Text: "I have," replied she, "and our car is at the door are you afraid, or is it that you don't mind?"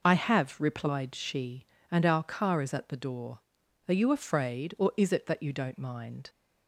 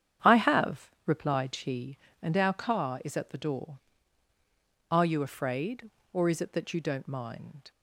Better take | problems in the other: first | starts louder than the rest; strong; until 1.7 s; 9 dB

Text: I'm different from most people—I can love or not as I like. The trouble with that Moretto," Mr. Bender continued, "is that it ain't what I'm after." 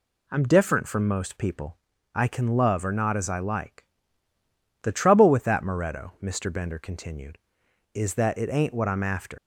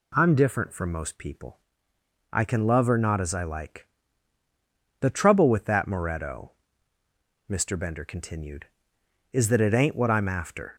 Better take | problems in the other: second | leaves "after" unfinished; at 9.3 s; 130 ms

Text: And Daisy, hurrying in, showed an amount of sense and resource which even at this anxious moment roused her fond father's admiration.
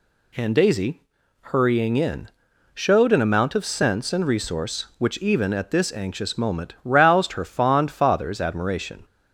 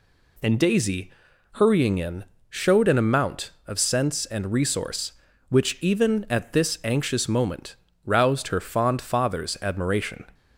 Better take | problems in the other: first | changes voice at "Daisy"; from 0.5 s on; 9.7 s long // pauses between "moment" and "roused"; slight; at 7.7 s; 0.30 s long

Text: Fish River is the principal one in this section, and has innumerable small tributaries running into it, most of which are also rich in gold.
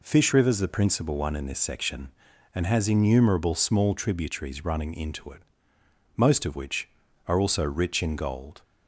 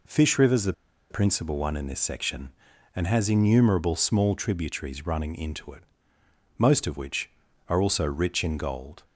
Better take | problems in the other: first | pauses between "the" and "principal"; at 0.7 s; 0.38 s long

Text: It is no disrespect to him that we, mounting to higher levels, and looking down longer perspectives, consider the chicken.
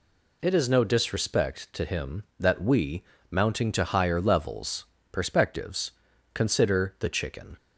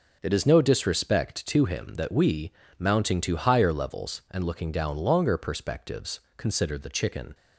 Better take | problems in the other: second | skips "and looking down longer"; at 4.9 s

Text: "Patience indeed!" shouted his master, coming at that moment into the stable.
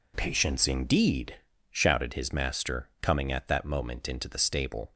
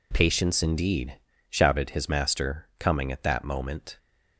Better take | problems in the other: first | stops before "into the stable"; at 3.9 s

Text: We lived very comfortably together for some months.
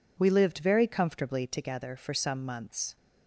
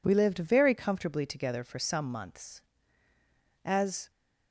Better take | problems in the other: first | goes on to say "As"; slight; from 3.6 s on; 0.46 s long

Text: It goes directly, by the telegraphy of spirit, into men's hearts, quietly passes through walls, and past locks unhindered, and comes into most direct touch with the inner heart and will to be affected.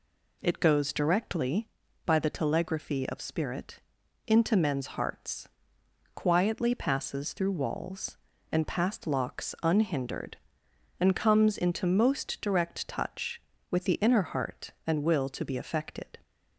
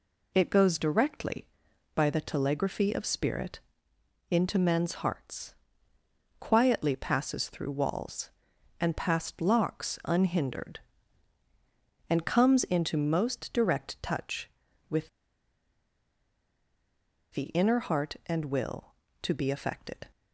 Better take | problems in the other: first | pauses between "with" and "the"; strong; at 15.0 s; 2.2 s long

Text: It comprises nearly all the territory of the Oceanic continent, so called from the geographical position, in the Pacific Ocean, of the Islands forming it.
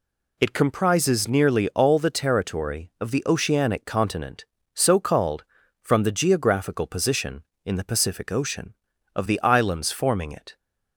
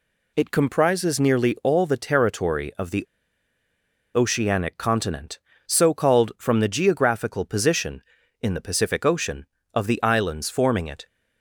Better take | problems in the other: first | pauses between "the" and "Oceanic"; at 3.0 s; 1.1 s long

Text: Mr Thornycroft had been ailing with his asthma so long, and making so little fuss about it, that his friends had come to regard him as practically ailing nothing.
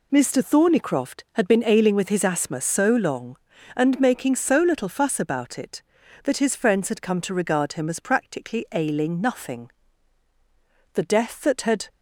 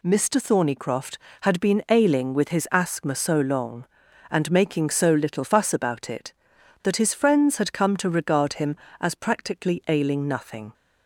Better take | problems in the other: second | goes on to say "The death that had"; noticeable; from 10.9 s on; 0.96 s long

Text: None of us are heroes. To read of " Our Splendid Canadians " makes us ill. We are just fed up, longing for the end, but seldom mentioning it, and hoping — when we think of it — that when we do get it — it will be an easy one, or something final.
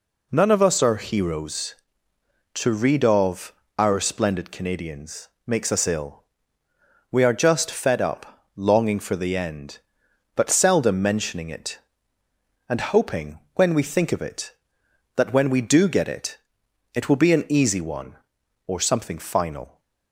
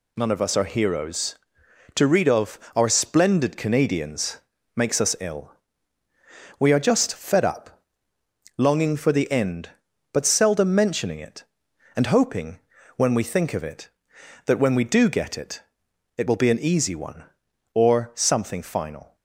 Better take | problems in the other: neither | none

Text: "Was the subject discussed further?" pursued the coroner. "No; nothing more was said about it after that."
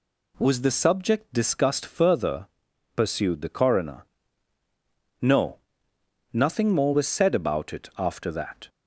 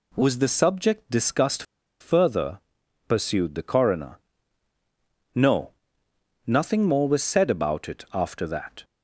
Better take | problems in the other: first | pauses between "discussed" and "further"; at 1.6 s; 0.37 s long

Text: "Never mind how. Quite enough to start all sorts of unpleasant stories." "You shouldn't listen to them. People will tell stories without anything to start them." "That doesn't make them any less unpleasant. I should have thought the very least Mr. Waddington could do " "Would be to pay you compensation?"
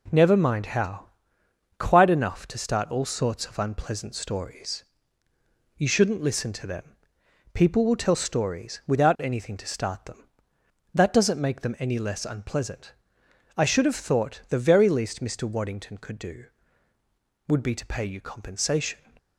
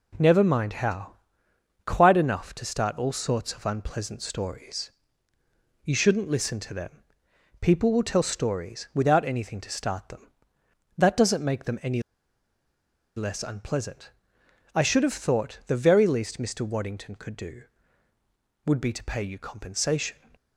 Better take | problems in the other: first | pauses between "any" and "less"; at 12.0 s; 1.1 s long

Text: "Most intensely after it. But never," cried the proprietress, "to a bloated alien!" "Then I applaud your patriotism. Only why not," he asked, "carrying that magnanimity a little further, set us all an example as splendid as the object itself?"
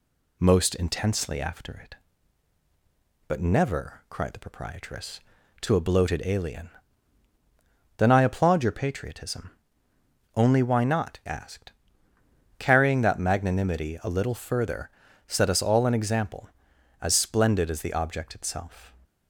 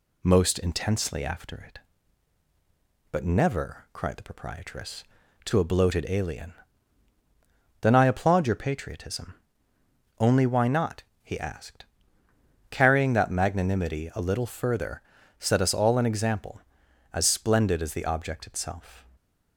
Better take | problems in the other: second | skips "he"; at 11.2 s

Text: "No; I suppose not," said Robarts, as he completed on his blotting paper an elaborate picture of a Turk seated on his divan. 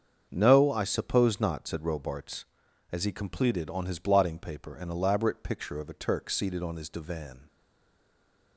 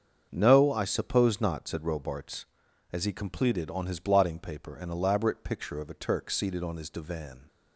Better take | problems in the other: second | starts louder than the rest; until 1.3 s; 7 dB; also in the second // stays silent after the last word; from 7.4 s on; 1.1 s long

